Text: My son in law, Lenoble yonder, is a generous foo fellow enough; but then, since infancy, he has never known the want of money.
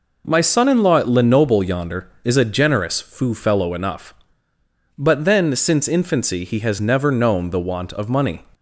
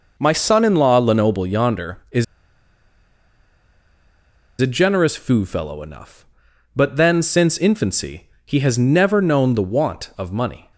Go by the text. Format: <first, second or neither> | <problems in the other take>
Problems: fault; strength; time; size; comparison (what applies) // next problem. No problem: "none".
first | pauses between "is" and "a"; strong; at 2.2 s; 2.3 s long